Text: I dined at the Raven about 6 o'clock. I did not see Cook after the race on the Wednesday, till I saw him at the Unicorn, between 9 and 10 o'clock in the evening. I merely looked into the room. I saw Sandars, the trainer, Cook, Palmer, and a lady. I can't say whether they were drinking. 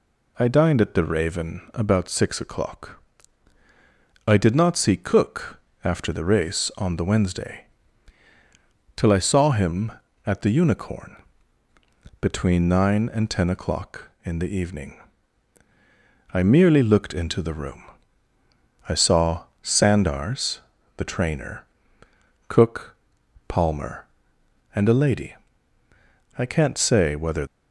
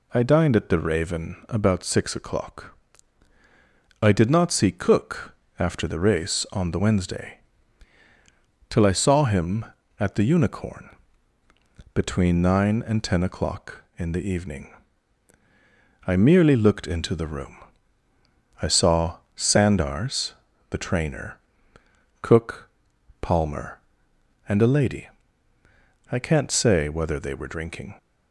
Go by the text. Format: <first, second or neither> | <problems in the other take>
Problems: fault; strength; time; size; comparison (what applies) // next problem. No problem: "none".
second | pauses between "Cook" and "after"; slight; at 5.5 s; 0.26 s long; slight in the second // pauses between "saw" and "Sandars"; slight; at 19.4 s; 0.18 s long; slight in the second // stops before "they were drinking"; at 27.4 s